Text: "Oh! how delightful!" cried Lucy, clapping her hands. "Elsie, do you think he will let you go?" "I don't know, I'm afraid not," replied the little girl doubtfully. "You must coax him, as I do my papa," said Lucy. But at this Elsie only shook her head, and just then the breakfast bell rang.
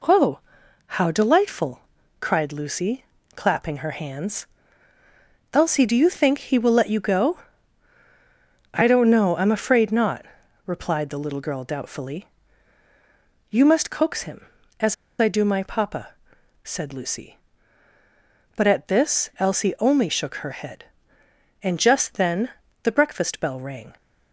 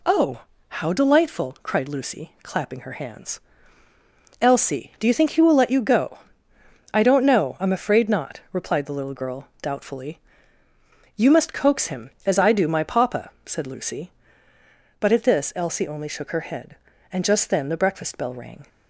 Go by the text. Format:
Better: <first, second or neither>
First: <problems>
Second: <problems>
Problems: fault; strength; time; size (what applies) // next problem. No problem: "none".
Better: second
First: pauses between "as" and "I"; slight; at 14.9 s; 0.25 s long // pauses between "then" and "the"; slight; at 22.4 s; 0.34 s long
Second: none